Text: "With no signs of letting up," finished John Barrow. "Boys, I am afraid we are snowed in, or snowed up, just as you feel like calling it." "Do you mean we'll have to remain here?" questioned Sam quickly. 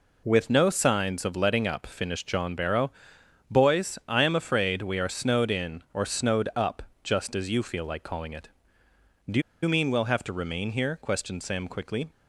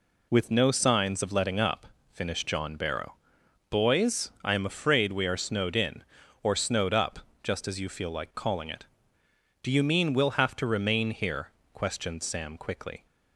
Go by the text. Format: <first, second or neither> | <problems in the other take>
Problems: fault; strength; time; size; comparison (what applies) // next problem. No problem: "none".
second | pauses between "Do" and "you"; slight; at 9.4 s; 0.21 s long